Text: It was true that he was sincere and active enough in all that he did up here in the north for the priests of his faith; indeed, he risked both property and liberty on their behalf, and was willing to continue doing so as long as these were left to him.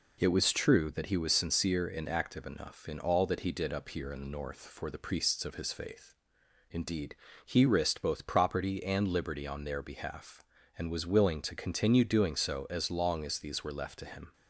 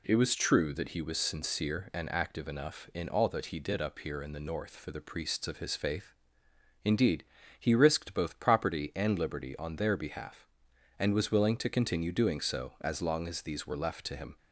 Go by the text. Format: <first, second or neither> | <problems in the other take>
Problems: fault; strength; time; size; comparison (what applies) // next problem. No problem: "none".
neither | none